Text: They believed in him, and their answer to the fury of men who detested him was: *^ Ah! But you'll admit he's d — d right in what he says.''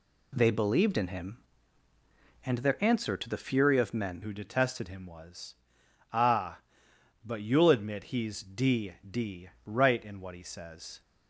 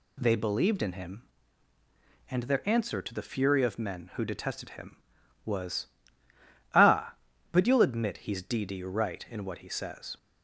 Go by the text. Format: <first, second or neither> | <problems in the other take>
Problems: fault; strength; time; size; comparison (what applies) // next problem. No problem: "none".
second | changes voice at "who"; from 4.2 s on; 6.8 s long // pauses between "d" and "right"; slight; at 9.4 s; 0.16 s long